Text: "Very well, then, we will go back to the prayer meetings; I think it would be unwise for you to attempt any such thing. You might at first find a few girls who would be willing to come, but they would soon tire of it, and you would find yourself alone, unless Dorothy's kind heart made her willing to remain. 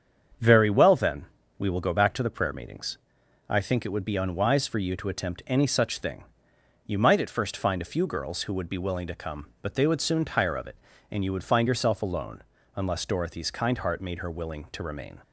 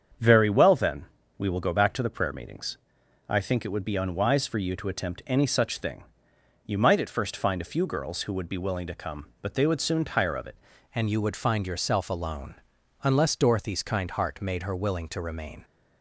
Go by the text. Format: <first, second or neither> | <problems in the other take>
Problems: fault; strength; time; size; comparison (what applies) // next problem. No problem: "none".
first | starts louder than the rest; strong; until 1.5 s; 7.5 dB; strong in the first // changes voice at "and"; from 10.9 s on; 4.7 s long